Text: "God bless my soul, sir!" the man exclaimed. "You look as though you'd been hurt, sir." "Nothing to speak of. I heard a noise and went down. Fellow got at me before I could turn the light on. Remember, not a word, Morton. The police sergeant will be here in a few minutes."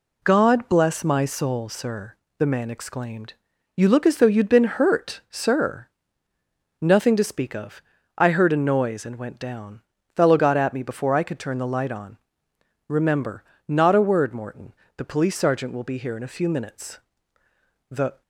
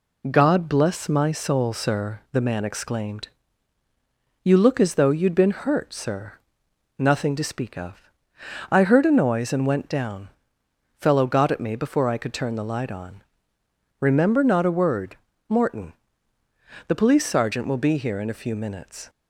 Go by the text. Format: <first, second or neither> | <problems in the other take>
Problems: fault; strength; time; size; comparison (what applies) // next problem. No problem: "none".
second | goes on to say "The"; slight; from 17.8 s on; 0.32 s long